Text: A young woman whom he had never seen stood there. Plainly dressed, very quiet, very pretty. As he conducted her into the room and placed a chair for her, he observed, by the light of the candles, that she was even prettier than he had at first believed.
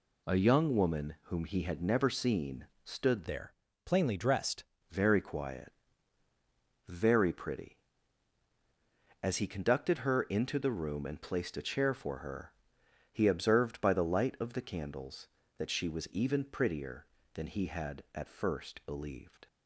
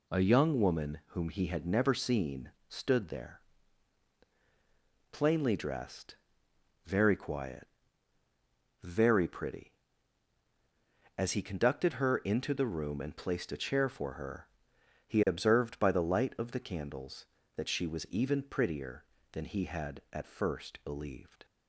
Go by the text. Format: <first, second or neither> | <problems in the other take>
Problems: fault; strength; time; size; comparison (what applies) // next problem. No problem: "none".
second | pauses between "seen" and "stood"; slight; at 2.6 s; 0.20 s long; slight in the second // changes voice from "there" to "dressed"; from 3.2 to 4.6 s; 1.4 s long